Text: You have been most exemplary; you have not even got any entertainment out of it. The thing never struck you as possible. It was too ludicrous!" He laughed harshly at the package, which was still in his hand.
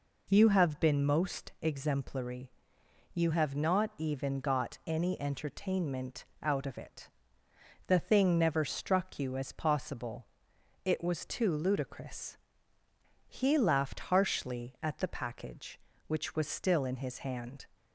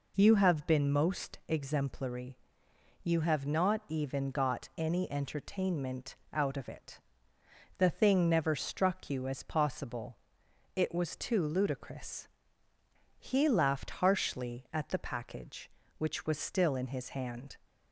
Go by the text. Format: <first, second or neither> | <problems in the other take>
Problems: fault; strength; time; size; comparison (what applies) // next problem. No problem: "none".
neither | pauses between "entertainment" and "out"; slight; the same in both